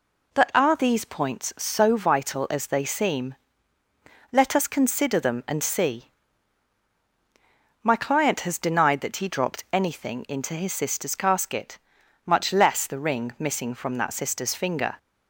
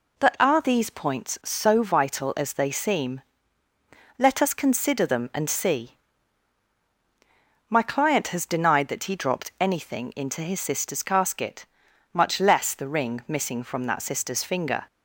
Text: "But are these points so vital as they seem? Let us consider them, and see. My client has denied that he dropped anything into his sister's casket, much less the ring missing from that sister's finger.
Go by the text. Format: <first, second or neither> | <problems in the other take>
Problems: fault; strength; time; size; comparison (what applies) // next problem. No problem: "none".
neither | none